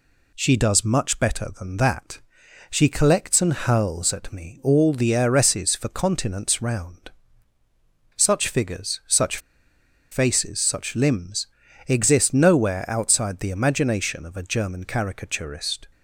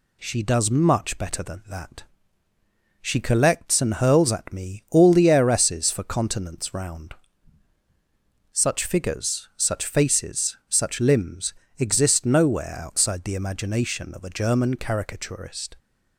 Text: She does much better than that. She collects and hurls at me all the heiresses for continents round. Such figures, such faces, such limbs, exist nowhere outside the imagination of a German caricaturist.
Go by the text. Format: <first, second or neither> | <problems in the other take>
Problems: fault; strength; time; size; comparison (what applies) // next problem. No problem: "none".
second | pauses between "such" and "faces"; noticeable; at 9.3 s; 0.73 s long